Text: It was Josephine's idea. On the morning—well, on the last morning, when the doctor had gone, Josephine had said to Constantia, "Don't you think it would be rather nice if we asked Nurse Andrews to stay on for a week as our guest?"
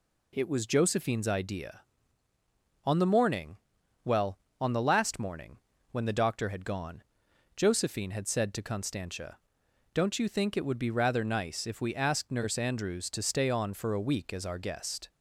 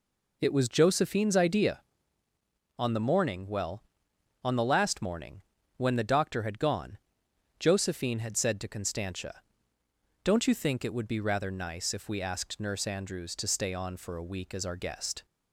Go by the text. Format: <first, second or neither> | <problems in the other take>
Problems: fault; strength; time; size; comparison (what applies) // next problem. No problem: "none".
neither | none